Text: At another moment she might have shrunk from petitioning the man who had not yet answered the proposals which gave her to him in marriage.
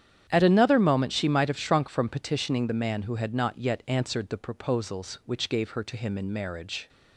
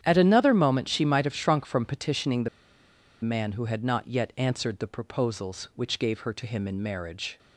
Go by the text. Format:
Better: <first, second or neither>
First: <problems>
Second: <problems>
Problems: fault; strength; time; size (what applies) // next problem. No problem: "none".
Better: first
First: starts louder than the rest; strong; until 1.3 s; 9 dB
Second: starts louder than the rest; strong; until 1.0 s; 9.5 dB // pauses between "the" and "man"; noticeable; at 2.4 s; 0.73 s long